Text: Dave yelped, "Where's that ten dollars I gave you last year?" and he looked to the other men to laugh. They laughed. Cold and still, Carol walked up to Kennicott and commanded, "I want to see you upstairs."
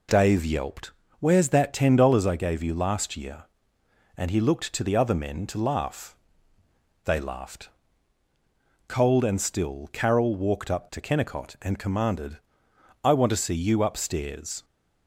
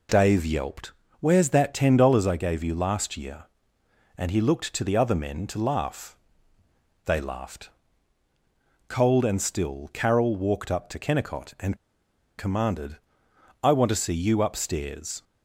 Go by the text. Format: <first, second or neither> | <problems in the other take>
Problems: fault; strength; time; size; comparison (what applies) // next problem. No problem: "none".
first | pauses between "and" and "commanded"; noticeable; at 11.7 s; 0.61 s long